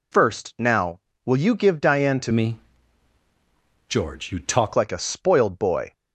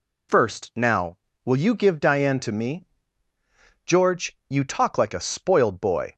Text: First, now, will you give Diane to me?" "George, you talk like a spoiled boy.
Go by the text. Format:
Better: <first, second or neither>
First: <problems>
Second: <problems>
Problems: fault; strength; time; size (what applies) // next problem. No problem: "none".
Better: second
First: changes voice from "me" to "talk"; from 2.3 to 4.7 s; 2.4 s long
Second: none